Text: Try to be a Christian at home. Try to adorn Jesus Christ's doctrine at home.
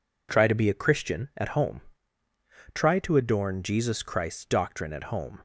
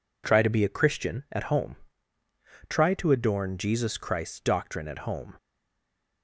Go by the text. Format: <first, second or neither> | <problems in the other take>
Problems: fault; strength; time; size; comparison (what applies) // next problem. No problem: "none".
first | stays silent after the last word; slight; from 5.3 s on; 0.9 s long